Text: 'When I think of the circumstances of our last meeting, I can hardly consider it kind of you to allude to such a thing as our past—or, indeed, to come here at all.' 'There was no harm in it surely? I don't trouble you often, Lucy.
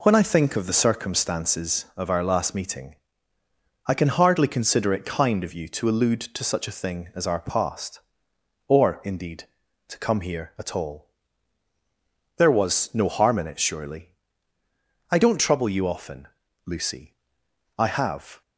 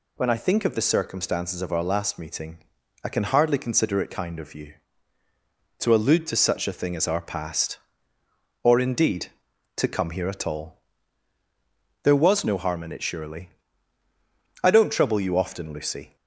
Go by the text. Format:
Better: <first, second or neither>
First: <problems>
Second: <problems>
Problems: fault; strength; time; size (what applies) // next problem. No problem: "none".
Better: second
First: goes on to say "I have"; noticeable; from 17.7 s on; 0.64 s long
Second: none